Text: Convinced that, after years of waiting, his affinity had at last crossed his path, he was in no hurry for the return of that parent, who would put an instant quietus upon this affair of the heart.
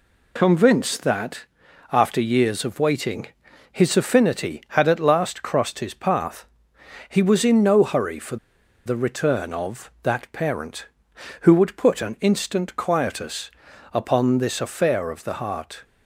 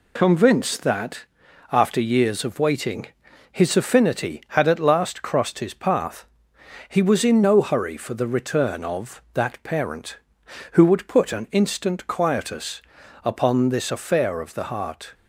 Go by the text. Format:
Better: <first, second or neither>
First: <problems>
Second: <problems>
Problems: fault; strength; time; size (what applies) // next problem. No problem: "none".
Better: second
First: pauses between "for" and "the"; noticeable; at 8.3 s; 0.49 s long // pauses between "quietus" and "upon"; at 13.4 s; 0.44 s long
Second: pauses between "quietus" and "upon"; at 12.8 s; 0.44 s long